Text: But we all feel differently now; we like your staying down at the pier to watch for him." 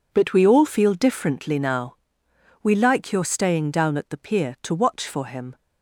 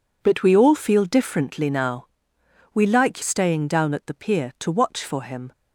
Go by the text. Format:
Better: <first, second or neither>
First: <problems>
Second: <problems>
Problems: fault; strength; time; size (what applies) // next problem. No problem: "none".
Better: first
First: none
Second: skips "your"; at 3.2 s